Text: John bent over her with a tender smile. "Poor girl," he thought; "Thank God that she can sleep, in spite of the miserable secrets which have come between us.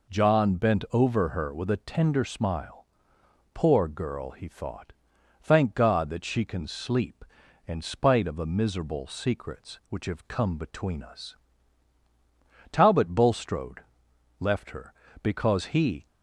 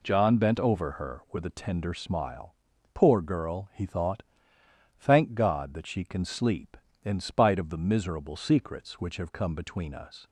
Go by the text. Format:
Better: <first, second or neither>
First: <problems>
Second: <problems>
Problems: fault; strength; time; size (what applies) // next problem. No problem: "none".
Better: second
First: goes on to say "Talbot Bulstrode left her because he"; strong; from 12.6 s on; 3.3 s long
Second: none